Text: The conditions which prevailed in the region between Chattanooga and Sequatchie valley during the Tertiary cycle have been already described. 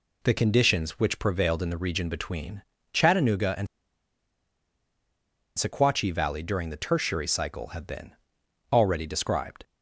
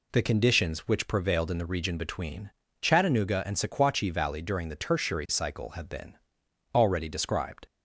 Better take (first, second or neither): second